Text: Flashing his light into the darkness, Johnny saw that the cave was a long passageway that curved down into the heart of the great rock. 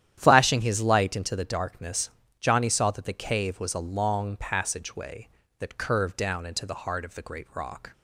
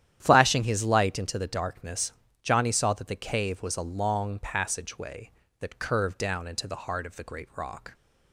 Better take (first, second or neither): neither